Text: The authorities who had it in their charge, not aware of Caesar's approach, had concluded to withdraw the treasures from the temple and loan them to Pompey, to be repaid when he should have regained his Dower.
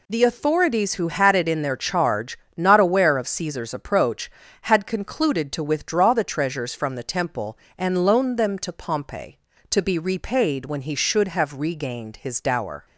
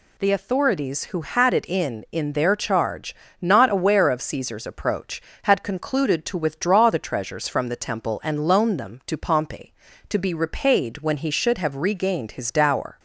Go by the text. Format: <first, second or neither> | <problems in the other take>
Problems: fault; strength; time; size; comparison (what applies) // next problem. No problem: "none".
first | says "in" twice; at 2.1 s